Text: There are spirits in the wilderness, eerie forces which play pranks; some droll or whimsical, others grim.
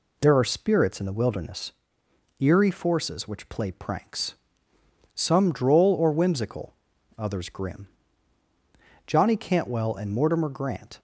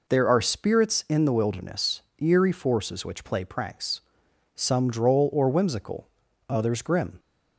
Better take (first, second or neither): second